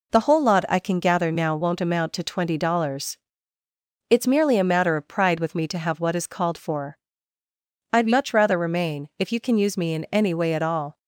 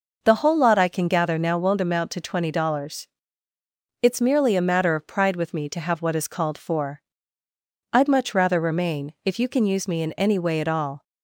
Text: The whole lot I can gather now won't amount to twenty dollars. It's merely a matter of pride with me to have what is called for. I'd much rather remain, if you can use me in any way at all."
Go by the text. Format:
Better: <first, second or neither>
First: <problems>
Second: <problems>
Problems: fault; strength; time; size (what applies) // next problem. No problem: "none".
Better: neither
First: none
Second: none